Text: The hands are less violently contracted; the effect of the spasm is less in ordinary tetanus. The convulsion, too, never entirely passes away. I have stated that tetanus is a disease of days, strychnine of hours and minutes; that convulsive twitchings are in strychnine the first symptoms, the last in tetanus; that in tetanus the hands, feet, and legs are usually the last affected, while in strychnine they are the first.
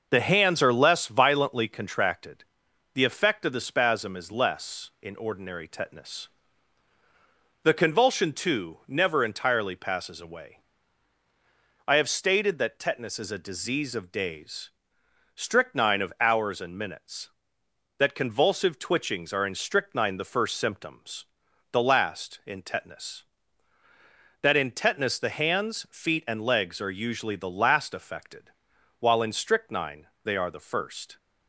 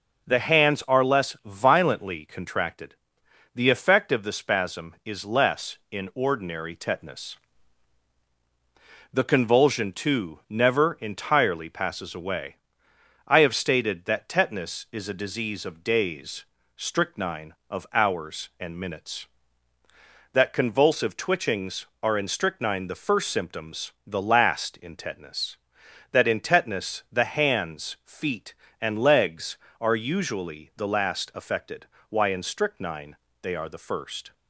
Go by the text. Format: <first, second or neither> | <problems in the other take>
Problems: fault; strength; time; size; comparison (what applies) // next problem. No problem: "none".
first | says "why" for "while"; at 32.0 s // pauses between "strychnine" and "they"; slight; at 33.1 s; 0.26 s long; slight in the first